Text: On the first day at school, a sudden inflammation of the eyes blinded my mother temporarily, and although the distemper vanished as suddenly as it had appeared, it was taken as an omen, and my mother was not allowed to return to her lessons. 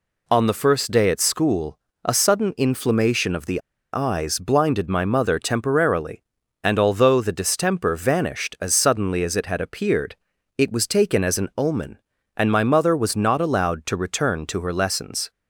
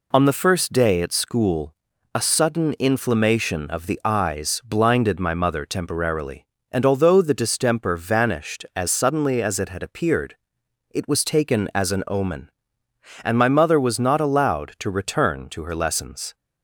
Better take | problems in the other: second | pauses between "the" and "eyes"; slight; at 3.6 s; 0.32 s long

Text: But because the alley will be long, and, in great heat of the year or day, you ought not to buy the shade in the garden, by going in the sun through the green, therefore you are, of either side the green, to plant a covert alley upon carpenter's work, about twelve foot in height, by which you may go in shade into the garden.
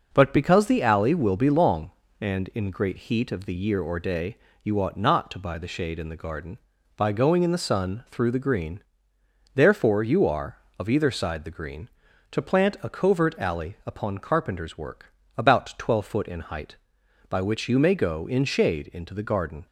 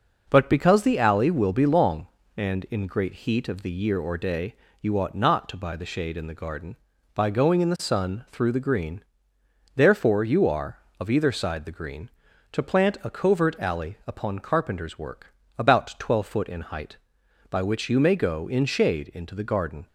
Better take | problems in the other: neither | none

